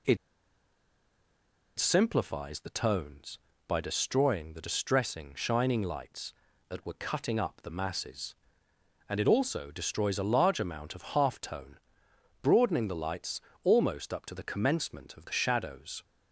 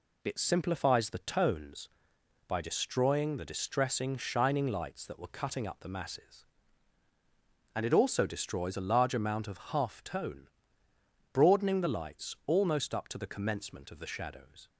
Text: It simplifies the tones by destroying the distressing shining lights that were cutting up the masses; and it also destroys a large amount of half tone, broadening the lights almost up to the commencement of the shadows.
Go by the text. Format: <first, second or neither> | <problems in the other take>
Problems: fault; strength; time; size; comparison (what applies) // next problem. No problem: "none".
second | pauses between "It" and "simplifies"; strong; at 0.1 s; 1.6 s long // pauses between "lights" and "almost"; slight; at 13.4 s; 0.22 s long